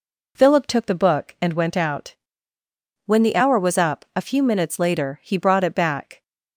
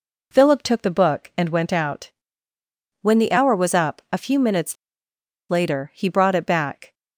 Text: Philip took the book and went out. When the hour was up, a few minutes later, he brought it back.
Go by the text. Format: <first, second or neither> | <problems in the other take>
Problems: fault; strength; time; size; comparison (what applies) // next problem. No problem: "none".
first | pauses between "minutes" and "later"; noticeable; at 4.7 s; 0.76 s long